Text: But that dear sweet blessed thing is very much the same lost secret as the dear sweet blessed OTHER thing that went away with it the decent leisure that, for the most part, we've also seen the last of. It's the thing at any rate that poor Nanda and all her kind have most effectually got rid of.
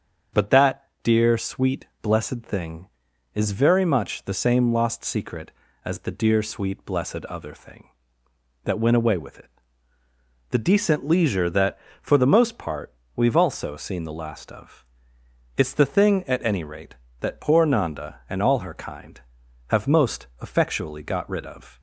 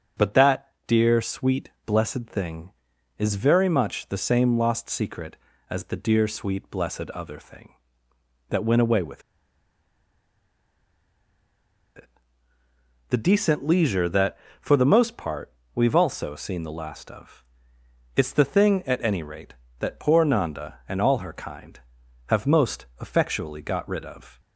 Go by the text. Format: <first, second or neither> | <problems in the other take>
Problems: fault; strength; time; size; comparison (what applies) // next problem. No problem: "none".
first | starts louder than the rest; until 1.3 s; 7 dB; also in the first // pauses between "that" and "dear"; slight; at 0.6 s; 0.18 s long; slight in the first // pauses between "sweet" and "blessed"; slight; at 1.6 s; 0.16 s long; slight in the first // pauses between "with" and "it"; strong; at 9.2 s; 2.7 s long // pauses between "it" and "the"; at 12.0 s; 1.0 s long; also in the first // pauses between "most" and "effectually"; slight; at 22.8 s; 0.16 s long; slight in the first